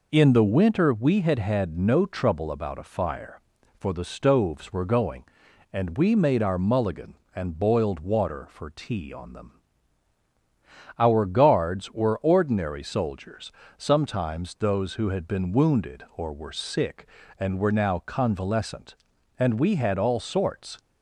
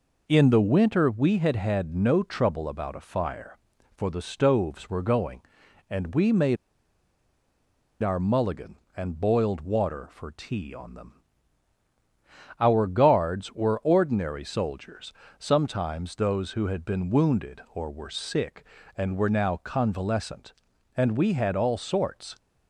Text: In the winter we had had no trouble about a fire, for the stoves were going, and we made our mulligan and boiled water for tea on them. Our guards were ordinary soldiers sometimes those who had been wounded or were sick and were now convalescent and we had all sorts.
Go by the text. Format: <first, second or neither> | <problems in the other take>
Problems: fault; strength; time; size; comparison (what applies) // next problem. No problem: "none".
first | pauses between "made" and "our"; strong; at 6.5 s; 1.4 s long // pauses between "soldiers" and "sometimes"; slight; at 15.1 s; 0.24 s long; slight in the first